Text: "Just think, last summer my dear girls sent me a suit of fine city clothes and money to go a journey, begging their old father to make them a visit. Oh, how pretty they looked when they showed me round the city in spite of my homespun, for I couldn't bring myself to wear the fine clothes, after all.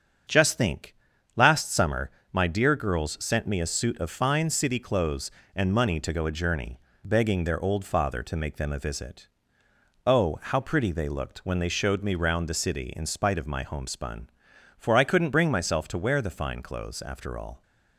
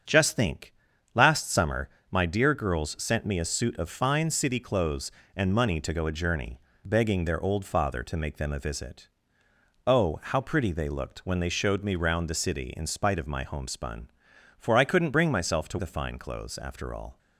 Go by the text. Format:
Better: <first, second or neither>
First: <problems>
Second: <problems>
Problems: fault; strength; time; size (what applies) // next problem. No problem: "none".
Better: first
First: starts louder than the rest; strong; until 1.7 s; 7.5 dB // pauses between "summer" and "my"; slight; at 2.0 s; 0.24 s long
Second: starts louder than the rest; strong; until 1.4 s; 7.5 dB // pauses between "summer" and "my"; slight; at 1.8 s; 0.24 s long // skips "wear"; at 15.7 s